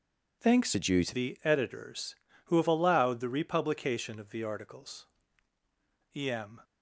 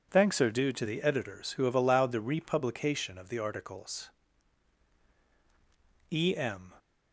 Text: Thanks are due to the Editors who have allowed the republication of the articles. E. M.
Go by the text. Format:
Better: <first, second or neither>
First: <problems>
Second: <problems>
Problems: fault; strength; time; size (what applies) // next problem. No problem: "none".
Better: second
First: changes voice from "are" to "to"; from 0.7 to 1.1 s; 0.4 s long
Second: none